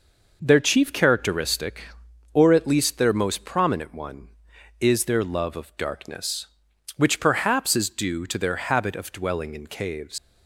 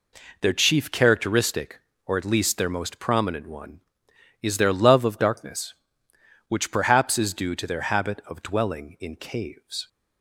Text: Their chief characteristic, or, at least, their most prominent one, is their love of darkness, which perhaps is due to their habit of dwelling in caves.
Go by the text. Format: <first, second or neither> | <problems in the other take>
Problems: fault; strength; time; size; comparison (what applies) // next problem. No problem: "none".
second | leaves "caves" unfinished; at 10.1 s; 105 ms